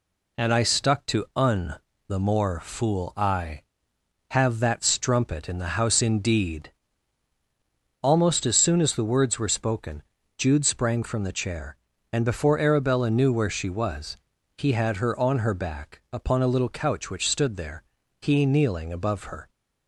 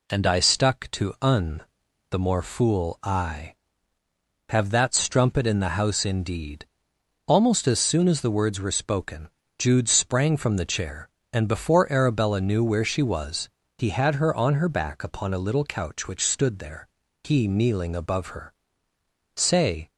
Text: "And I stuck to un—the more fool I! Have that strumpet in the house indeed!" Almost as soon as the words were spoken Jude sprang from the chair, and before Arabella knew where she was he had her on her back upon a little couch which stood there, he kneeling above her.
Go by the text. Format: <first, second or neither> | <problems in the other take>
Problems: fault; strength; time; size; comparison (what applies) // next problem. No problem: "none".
first | pauses between "spoken" and "Jude"; slight; at 9.2 s; 0.28 s long; also in the first // pauses between "was" and "he"; slight; at 13.4 s; 0.30 s long; also in the first // goes on to say "Say"; from 19.3 s on; 0.54 s long